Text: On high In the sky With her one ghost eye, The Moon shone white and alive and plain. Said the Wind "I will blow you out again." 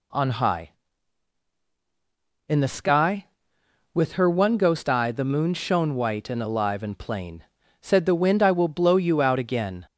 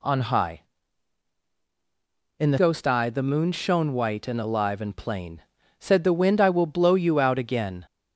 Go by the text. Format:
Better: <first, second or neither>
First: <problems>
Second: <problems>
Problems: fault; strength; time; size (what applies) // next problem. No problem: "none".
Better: first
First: none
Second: skips "sky With her one"; at 2.5 s